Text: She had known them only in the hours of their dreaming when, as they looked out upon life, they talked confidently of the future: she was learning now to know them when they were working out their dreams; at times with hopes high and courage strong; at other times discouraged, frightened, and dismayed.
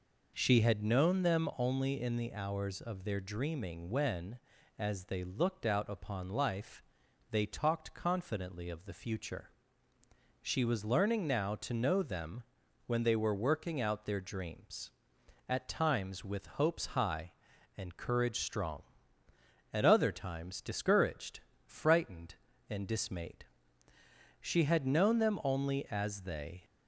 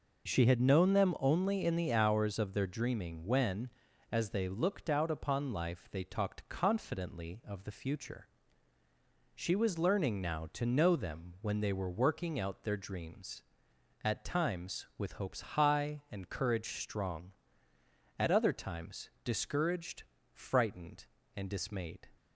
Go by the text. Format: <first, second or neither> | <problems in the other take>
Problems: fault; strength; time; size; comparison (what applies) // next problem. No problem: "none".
second | pauses between "them" and "when"; at 12.4 s; 0.44 s long // goes on to say "She had known them only as they"; strong; from 24.4 s on; 2.2 s long